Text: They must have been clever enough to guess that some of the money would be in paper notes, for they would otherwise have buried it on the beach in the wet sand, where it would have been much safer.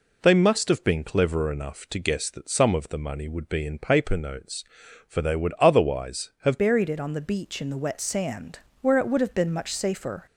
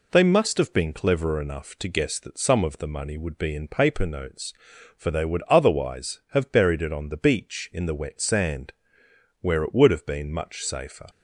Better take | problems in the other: second | changes voice at "buried"; from 6.5 s on; 3.7 s long

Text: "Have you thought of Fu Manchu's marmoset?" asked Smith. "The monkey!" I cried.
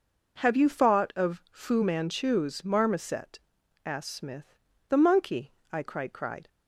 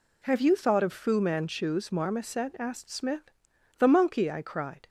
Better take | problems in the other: second | says "cried" twice; at 6.1 s

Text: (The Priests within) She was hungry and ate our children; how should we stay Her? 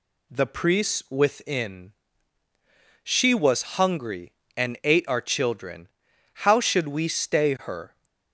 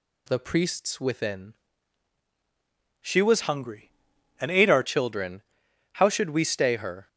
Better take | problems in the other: first | changes voice from "hungry" to "our"; from 3.4 to 4.8 s; 1.4 s long

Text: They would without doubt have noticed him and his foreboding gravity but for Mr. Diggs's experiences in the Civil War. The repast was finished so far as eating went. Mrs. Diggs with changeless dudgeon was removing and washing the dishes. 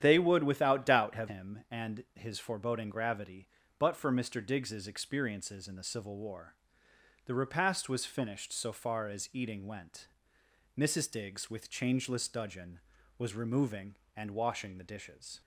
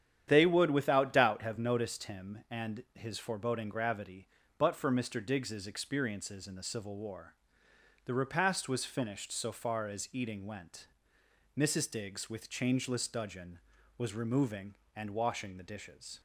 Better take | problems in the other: second | starts louder than the rest; strong; until 1.0 s; 10 dB; strong in the second // skips "noticed"; at 1.2 s

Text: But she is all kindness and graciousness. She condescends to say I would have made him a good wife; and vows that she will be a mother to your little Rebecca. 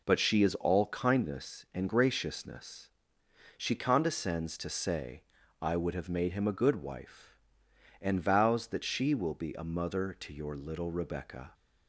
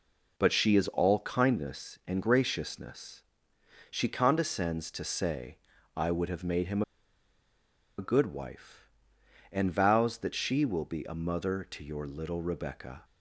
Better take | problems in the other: first | pauses between "say" and "I"; at 5.5 s; 0.38 s long; also in the first // pauses between "him" and "a"; at 6.8 s; 1.1 s long

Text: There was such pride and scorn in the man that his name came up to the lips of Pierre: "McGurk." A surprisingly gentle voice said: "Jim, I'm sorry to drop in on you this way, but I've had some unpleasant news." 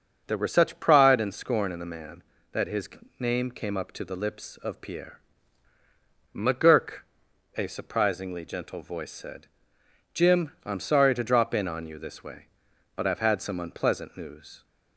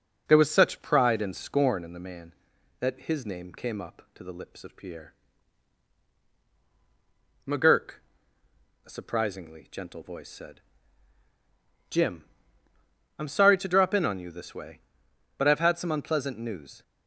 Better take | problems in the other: second | says "were" for "was"; at 0.3 s // pauses between "his" and "name"; slight; at 2.8 s; 0.32 s long

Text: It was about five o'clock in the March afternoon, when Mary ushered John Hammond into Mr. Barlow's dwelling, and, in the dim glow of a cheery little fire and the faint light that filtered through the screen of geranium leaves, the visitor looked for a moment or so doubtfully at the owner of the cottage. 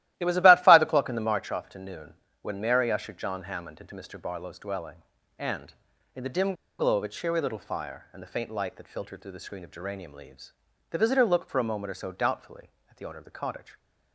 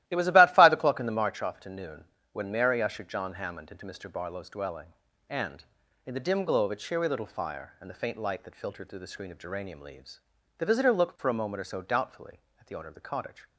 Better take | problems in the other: second | starts louder than the rest; strong; until 1.1 s; 15 dB; strong in the second // pauses between "dim" and "glow"; slight; at 6.5 s; 0.26 s long

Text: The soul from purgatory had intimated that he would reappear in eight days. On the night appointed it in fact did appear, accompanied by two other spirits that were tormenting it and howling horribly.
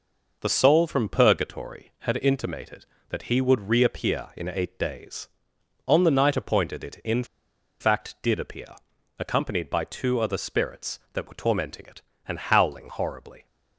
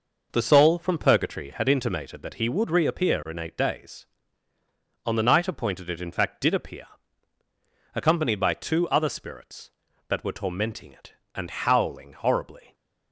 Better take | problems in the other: second | pauses between "in" and "fact"; noticeable; at 7.2 s; 0.56 s long

